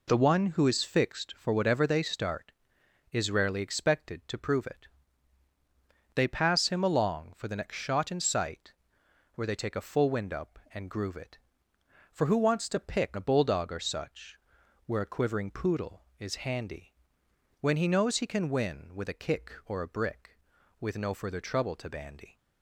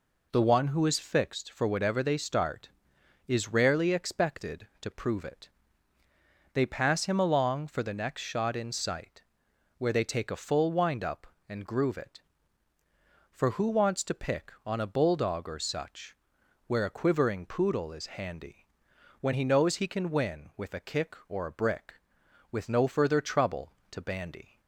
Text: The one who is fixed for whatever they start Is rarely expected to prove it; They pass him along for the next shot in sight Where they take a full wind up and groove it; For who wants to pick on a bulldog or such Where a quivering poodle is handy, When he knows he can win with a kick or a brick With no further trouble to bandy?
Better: second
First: pauses between "sight" and "Where"; noticeable; at 8.7 s; 0.62 s long // skips "on"; at 13.1 s // pauses between "such" and "Where"; noticeable; at 14.3 s; 0.48 s long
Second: pauses between "sight" and "Where"; noticeable; at 9.2 s; 0.56 s long // pauses between "such" and "Where"; noticeable; at 16.1 s; 0.52 s long

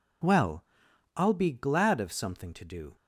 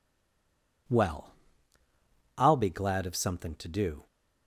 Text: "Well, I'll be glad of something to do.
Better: first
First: none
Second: stays silent before the first word; slight; until 0.8 s; 0.8 s long

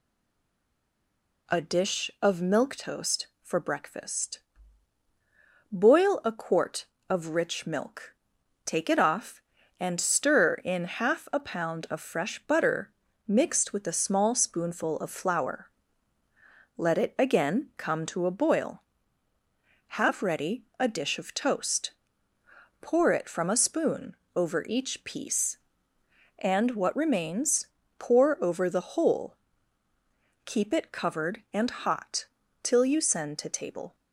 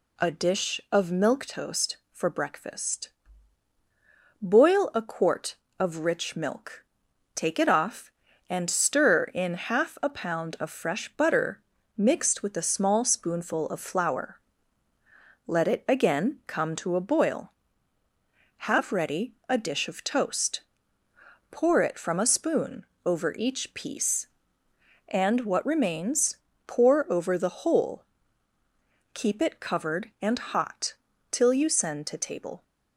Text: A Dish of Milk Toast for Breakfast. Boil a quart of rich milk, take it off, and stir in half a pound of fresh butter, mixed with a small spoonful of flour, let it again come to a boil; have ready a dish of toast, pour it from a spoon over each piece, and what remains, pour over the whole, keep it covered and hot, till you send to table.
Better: second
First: stays silent before the first word; noticeable; until 1.4 s; 1.4 s long // pauses between "spoon" and "over"; slight; at 24.1 s; 0.20 s long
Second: pauses between "spoon" and "over"; slight; at 22.8 s; 0.20 s long

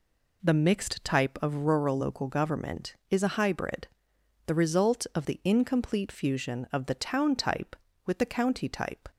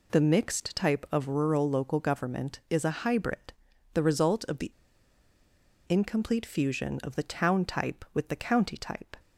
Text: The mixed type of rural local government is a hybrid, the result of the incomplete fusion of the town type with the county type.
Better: first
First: none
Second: pauses between "the" and "incomplete"; at 4.7 s; 1.1 s long

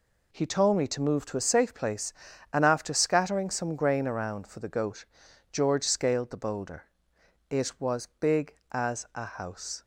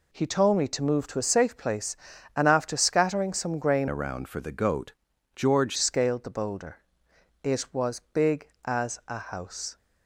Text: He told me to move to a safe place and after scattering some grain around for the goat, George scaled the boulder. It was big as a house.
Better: first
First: none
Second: changes voice from "around" to "George"; from 3.8 to 5.7 s; 1.9 s long

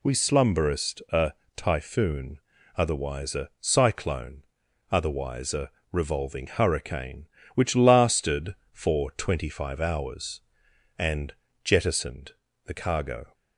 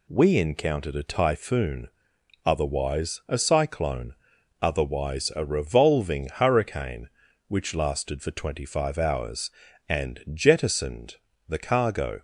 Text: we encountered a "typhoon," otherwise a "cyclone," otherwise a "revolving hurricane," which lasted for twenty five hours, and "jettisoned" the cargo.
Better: second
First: says "slumberest" for "encountered"; at 0.1 s // pauses between "a" and "typhoon"; slight; at 1.3 s; 0.24 s long // pauses between "a" and "revolving"; slight; at 5.6 s; 0.22 s long // pauses between "and" and "jettisoned"; slight; at 11.3 s; 0.32 s long // pauses between "jettisoned" and "the"; slight; at 12.3 s; 0.34 s long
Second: pauses between "jettisoned" and "the"; slight; at 11.1 s; 0.32 s long

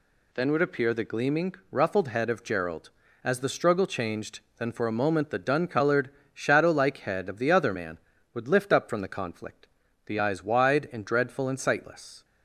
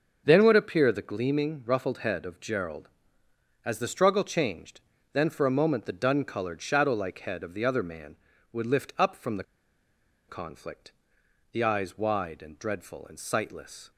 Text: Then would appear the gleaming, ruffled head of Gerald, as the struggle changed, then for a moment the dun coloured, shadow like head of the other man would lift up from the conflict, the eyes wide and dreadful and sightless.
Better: first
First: none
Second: starts louder than the rest; until 1.2 s; 6.5 dB // pauses between "the" and "conflict"; noticeable; at 9.4 s; 0.84 s long

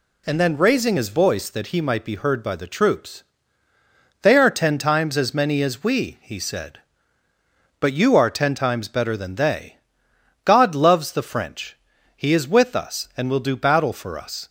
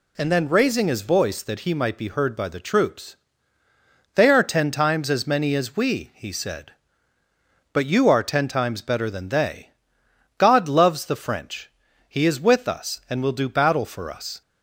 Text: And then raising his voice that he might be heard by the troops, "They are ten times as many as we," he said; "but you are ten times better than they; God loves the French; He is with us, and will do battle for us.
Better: neither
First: none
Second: none

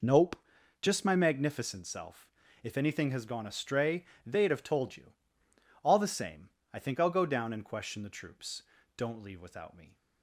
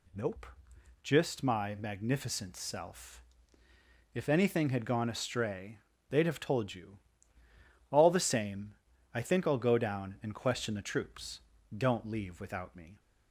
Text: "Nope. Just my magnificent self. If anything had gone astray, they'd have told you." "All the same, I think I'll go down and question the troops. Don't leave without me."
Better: second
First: says "has" for "had"; at 3.1 s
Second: none

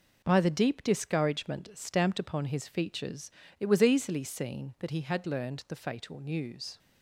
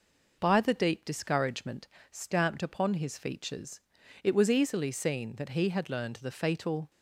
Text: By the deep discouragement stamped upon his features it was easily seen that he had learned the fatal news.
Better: first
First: pauses between "features" and "it"; slight; at 3.3 s; 0.26 s long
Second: pauses between "discouragement" and "stamped"; slight; at 1.8 s; 0.24 s long // pauses between "features" and "it"; at 3.8 s; 0.44 s long // stops before "news"; at 6.9 s

